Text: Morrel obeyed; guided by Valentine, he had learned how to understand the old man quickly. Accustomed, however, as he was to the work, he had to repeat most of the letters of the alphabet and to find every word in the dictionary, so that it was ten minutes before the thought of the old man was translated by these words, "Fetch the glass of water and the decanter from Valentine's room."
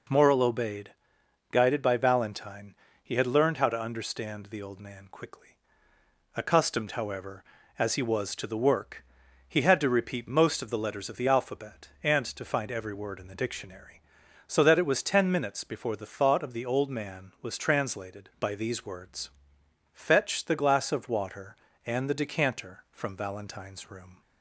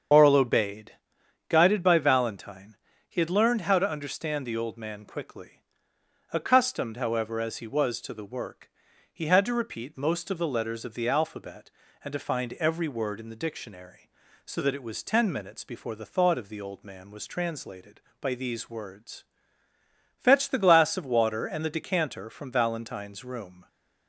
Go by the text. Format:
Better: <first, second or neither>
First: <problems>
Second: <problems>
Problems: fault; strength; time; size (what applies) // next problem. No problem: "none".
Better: first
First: none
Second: loses the start of "Morrel"; at 0.1 s; 60 ms // starts louder than the rest; strong; until 1.6 s; 7 dB